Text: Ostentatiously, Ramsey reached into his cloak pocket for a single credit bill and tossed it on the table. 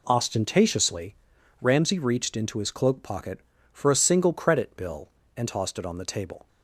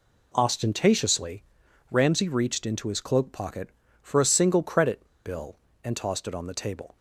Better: first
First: none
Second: pauses between "credit" and "bill"; slight; at 5.0 s; 0.20 s long

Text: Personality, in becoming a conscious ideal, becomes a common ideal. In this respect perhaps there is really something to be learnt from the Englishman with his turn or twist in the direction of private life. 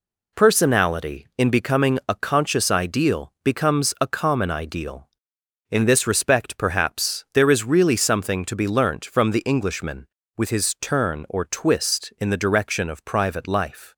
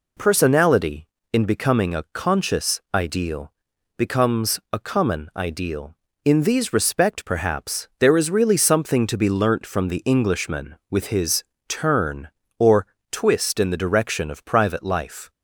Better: first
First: none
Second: says "these" for "this"; at 6.4 s // pauses between "his" and "turn"; slight; at 11.4 s; 0.24 s long // pauses between "or" and "twist"; slight; at 12.8 s; 0.24 s long

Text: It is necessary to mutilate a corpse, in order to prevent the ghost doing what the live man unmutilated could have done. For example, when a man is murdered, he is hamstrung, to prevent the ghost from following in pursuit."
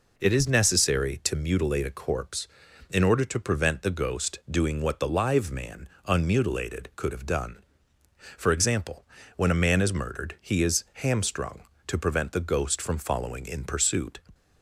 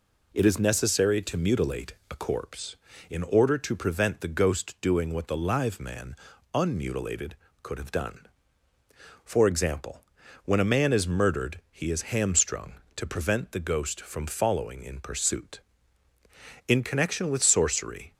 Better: first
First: pauses between "man" and "unmutilated"; slight; at 5.8 s; 0.18 s long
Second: pauses between "mutilate" and "a"; slight; at 1.9 s; 0.16 s long // pauses between "man" and "unmutilated"; at 6.1 s; 0.38 s long // goes on to say "In connection with sorcery"; from 16.6 s on; 1.4 s long

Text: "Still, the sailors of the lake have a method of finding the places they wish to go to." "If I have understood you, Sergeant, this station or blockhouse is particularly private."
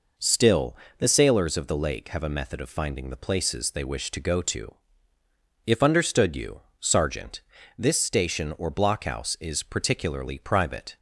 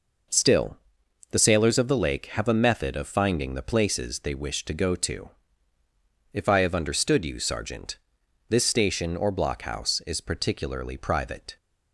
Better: second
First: skips "I have"; at 5.8 s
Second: none

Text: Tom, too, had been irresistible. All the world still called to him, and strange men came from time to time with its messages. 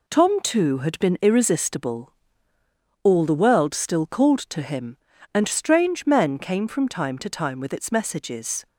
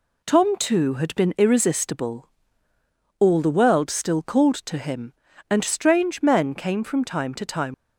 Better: first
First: none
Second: stops before "with its messages"; at 7.7 s

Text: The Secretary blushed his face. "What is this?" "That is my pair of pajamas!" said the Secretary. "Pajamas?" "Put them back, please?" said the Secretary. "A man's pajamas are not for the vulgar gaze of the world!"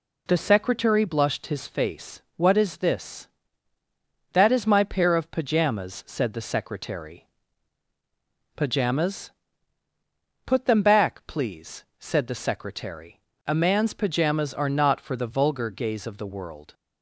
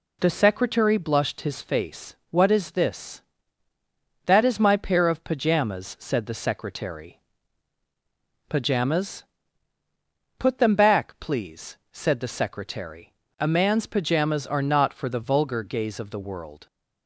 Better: neither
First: none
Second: none

